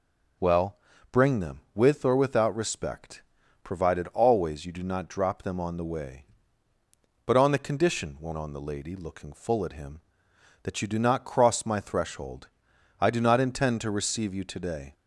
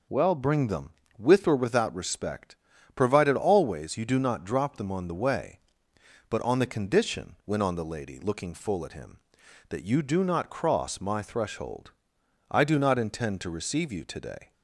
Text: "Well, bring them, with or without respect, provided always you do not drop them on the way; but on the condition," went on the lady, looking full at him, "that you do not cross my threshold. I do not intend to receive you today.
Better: neither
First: none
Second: none

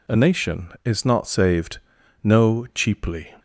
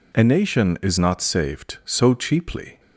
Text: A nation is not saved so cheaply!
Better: second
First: says "no" for "so"; at 2.2 s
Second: none

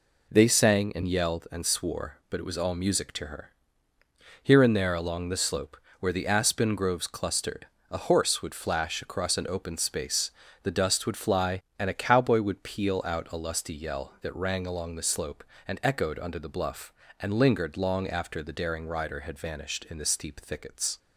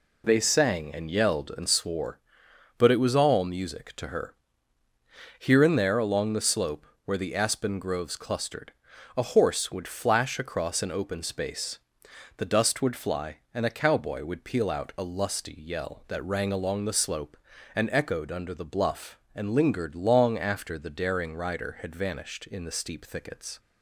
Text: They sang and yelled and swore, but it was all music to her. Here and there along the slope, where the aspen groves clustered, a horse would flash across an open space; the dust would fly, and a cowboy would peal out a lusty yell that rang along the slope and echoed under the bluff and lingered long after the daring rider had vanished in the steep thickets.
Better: neither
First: none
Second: none

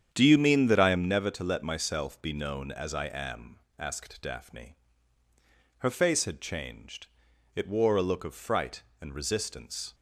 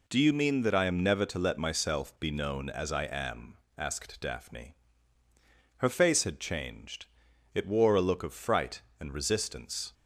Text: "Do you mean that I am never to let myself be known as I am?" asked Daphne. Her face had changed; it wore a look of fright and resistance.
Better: second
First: starts louder than the rest; strong; until 1.1 s; 8.5 dB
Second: none

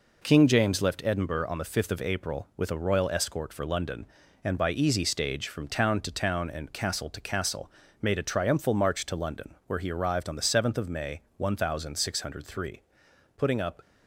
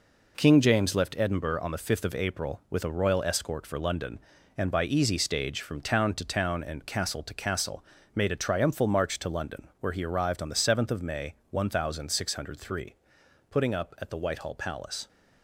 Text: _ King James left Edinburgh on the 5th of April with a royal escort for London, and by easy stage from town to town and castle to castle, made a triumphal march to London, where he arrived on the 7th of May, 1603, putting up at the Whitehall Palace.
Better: second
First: stops before "at the Whitehall Palace"; at 13.8 s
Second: none

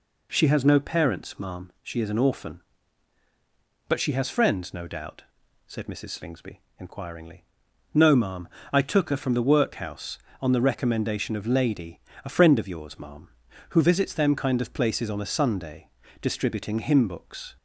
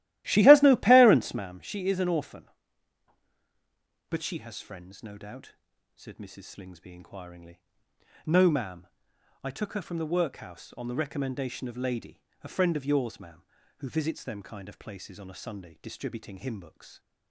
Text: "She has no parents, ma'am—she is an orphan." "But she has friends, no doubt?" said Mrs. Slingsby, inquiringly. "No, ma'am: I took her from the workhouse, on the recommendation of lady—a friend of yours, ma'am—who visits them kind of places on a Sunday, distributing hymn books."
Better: first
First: none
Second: starts louder than the rest; strong; until 1.5 s; 15 dB

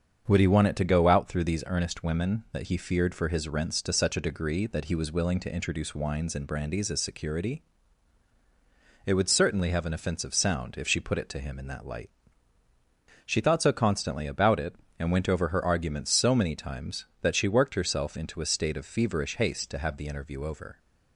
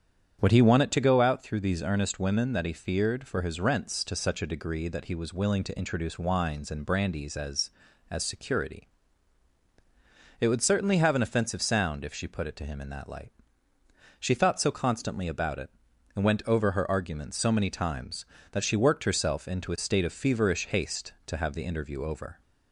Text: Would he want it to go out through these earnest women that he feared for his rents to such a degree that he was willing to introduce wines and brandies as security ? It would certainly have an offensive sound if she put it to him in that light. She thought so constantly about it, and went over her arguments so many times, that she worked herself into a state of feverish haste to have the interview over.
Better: first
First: starts louder than the rest; until 1.3 s; 7 dB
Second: starts louder than the rest; strong; until 1.4 s; 8.5 dB // says "as" twice; at 8.0 s

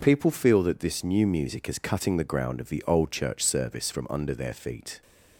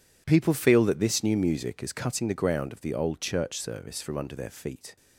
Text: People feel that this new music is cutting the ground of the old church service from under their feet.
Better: neither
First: none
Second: none

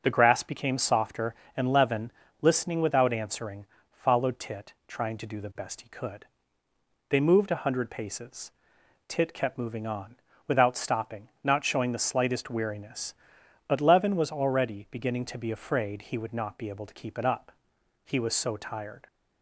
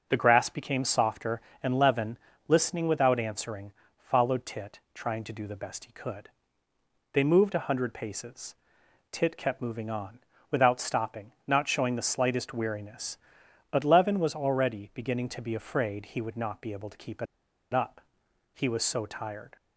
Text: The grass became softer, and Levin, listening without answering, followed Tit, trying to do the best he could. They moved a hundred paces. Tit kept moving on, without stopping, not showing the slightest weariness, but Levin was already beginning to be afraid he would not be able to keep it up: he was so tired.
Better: first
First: none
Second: pauses between "it" and "up"; noticeable; at 17.2 s; 0.48 s long

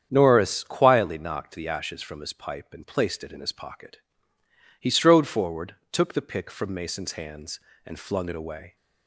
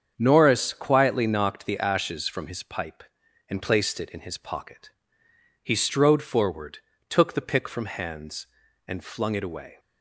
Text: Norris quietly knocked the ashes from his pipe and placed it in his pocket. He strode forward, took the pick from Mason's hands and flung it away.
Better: first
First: starts louder than the rest; strong; until 1.1 s; 8.5 dB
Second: starts louder than the rest; strong; until 1.1 s; 7.5 dB // skips "Mason's"; at 7.8 s

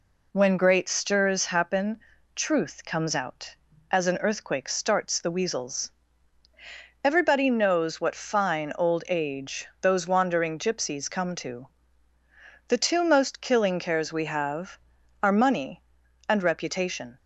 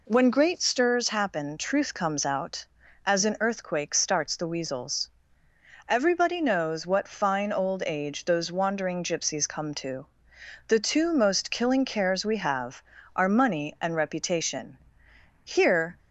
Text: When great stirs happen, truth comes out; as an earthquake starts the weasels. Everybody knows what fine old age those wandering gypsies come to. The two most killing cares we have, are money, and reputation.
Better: first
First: none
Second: goes on to say "Here"; from 15.4 s on; 0.54 s long

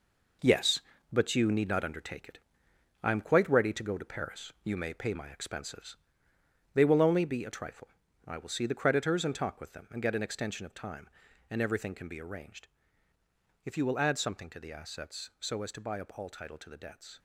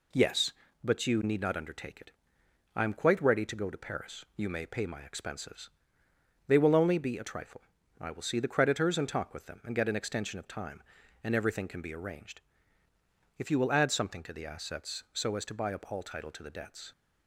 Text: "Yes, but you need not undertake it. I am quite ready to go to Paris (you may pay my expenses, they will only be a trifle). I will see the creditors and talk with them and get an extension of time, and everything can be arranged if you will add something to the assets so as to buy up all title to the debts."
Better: second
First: gets quieter; strong; throughout; 8.5 dB // pauses between "arranged" and "if"; noticeable; at 12.6 s; 0.96 s long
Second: pauses between "arranged" and "if"; noticeable; at 12.4 s; 0.96 s long

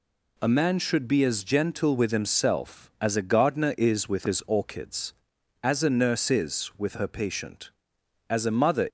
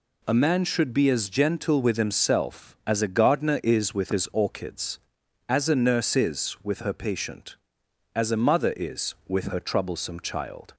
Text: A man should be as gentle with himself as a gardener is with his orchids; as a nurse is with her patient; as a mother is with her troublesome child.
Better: second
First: stops before "is with her troublesome child"; at 8.8 s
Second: none

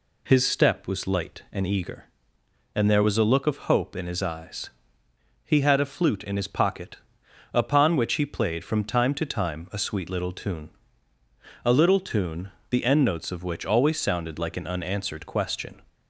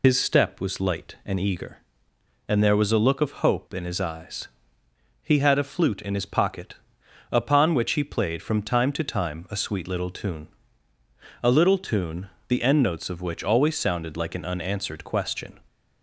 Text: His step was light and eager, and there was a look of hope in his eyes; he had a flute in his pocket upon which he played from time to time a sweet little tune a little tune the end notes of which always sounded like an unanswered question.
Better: first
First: pauses between "pocket" and "upon"; noticeable; at 6.9 s; 0.58 s long // pauses between "tune" and "a"; noticeable; at 10.6 s; 0.94 s long // pauses between "tune" and "the"; slight; at 12.4 s; 0.22 s long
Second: loses the start of "His"; at 0.0 s; 60 ms // pauses between "pocket" and "upon"; noticeable; at 6.7 s; 0.58 s long // pauses between "tune" and "a"; noticeable; at 10.4 s; 0.94 s long // pauses between "tune" and "the"; slight; at 12.2 s; 0.22 s long

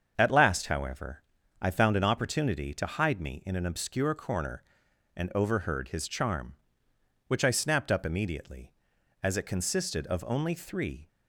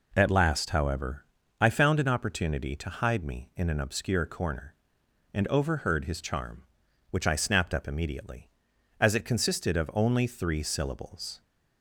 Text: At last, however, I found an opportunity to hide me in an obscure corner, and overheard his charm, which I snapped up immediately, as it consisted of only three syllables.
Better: second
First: starts louder than the rest; until 1.1 s; 7 dB // stops before "syllables"; at 11.0 s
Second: none

